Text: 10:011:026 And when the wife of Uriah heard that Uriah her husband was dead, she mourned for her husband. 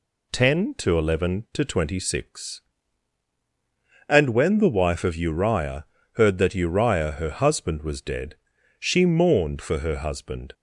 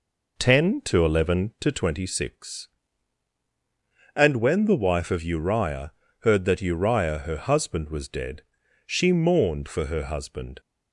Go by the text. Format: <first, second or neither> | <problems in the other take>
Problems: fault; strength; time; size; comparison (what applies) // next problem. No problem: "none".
first | starts louder than the rest; noticeable; until 1.9 s; 4.5 dB // pauses between "Uriah" and "heard"; slight; at 5.9 s; 0.28 s long; slight in the first